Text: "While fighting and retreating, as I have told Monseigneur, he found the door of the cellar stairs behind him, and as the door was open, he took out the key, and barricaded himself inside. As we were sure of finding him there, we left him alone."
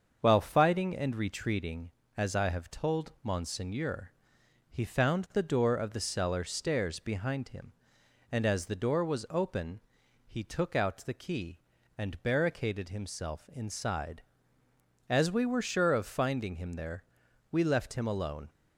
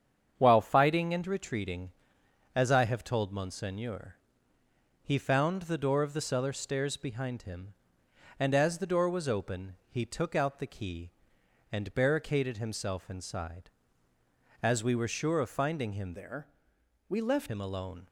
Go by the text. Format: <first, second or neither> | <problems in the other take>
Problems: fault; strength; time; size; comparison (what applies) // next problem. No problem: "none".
first | starts louder than the rest; strong; until 1.3 s; 8 dB; also in the first // changes voice from "there" to "left"; from 16.1 to 17.4 s; 1.3 s long